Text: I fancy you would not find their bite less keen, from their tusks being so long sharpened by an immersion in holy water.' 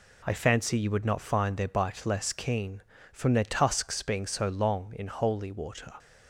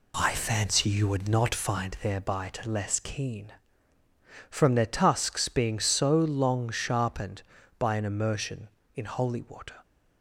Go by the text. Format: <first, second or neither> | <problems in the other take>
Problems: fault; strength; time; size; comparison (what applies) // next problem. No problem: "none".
second | skips "sharpened by an immersion"; at 4.9 s